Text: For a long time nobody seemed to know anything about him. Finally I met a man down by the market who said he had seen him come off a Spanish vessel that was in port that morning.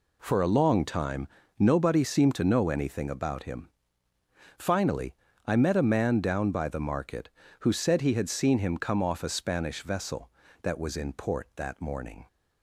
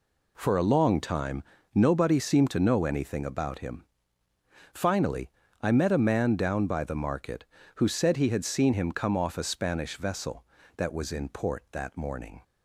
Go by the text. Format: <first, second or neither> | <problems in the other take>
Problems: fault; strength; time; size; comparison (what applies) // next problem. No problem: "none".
neither | pauses between "time" and "nobody"; slight; the same in both // pauses between "Finally" and "I"; slight; the same in both